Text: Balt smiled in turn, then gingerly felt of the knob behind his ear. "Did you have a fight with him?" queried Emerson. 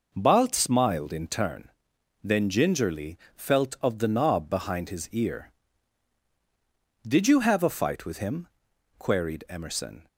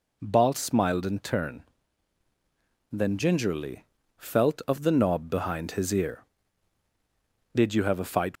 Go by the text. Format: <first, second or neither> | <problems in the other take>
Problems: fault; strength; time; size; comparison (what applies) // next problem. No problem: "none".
first | pauses between "gingerly" and "felt"; slight; at 3.8 s; 0.32 s long; slight in the first // stops before "with him queried Emerson"; at 8.3 s